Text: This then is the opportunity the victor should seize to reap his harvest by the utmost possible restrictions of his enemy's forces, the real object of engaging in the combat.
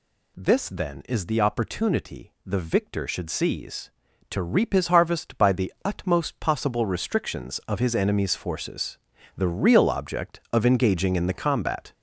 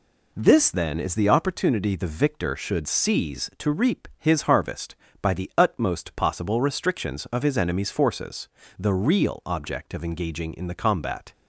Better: second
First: gets louder; throughout; 7 dB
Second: none

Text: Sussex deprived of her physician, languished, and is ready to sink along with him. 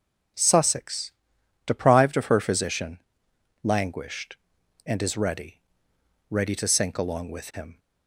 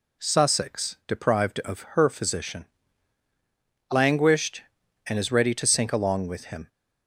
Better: second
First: pauses between "Sussex" and "deprived"; noticeable; at 1.1 s; 0.52 s long // says "ready" twice; at 6.3 s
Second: none

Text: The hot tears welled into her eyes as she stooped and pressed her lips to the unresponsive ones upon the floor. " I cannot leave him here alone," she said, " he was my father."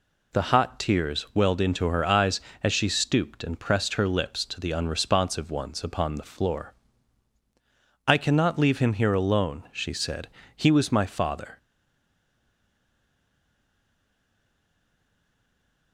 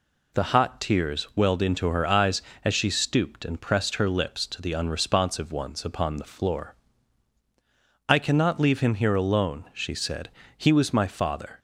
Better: second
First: stays silent after the last word; strong; from 11.5 s on; 4.4 s long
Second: none

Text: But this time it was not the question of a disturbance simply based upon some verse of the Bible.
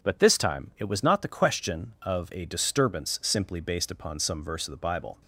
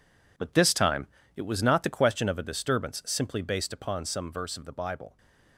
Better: first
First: none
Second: gets quieter; strong; throughout; 10 dB // pauses between "time" and "it"; slight; at 1.0 s; 0.28 s long

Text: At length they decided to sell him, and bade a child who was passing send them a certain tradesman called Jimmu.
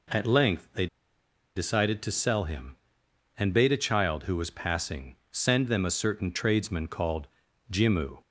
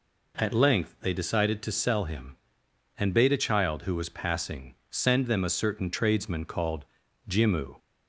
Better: second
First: pauses between "they" and "decided"; noticeable; at 0.8 s; 0.69 s long // pauses between "passing" and "send"; slight; at 5.1 s; 0.16 s long // pauses between "called" and "Jimmu"; at 7.2 s; 0.44 s long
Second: pauses between "passing" and "send"; slight; at 4.7 s; 0.16 s long // pauses between "called" and "Jimmu"; at 6.8 s; 0.44 s long

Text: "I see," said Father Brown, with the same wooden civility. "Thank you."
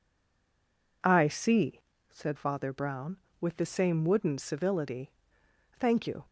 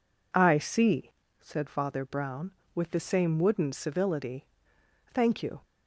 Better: second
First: stays silent before the first word; until 1.0 s; 1.0 s long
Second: none

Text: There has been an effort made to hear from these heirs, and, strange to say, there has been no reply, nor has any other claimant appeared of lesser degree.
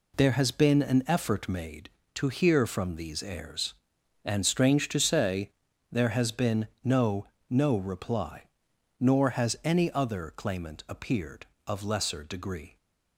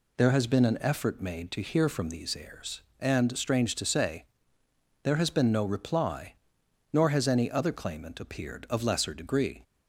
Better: second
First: pauses between "been" and "no"; slight; at 6.6 s; 0.16 s long // says "no" twice; at 7.4 s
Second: none

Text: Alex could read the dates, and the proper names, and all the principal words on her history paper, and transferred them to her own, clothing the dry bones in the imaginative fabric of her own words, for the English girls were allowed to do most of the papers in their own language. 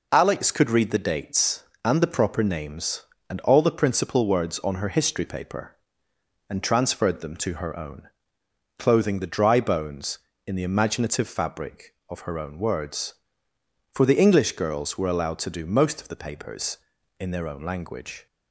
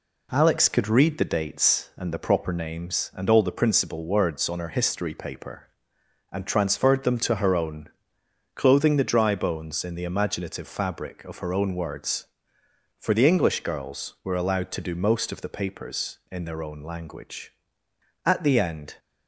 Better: first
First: none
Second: goes on to say "At the end"; noticeable; from 18.2 s on; 0.72 s long

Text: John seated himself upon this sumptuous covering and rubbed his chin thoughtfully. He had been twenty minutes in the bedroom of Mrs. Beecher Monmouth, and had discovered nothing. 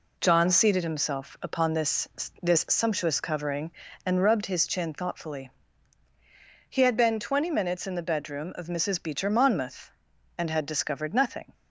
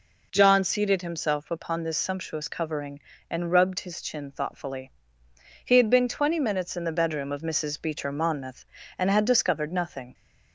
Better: second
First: says "this" twice; at 2.4 s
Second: none

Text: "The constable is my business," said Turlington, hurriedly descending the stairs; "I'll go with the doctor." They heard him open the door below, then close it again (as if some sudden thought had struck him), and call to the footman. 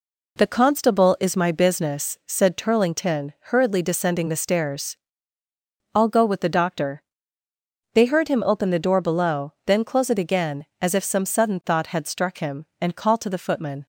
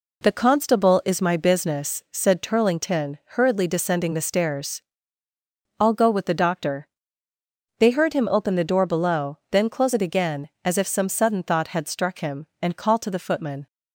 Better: neither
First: none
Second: none

